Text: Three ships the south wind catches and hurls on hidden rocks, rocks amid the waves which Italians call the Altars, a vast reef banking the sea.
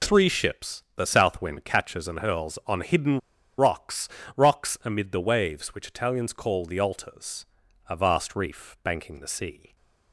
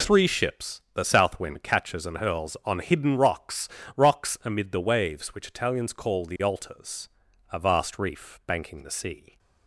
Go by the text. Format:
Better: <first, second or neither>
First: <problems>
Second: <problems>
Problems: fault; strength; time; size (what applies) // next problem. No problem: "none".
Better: second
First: pauses between "hidden" and "rocks"; at 3.1 s; 0.39 s long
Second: none